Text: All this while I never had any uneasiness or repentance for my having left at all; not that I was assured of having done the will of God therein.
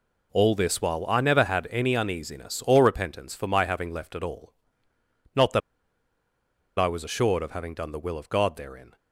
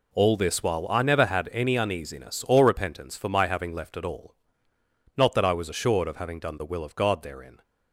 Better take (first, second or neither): second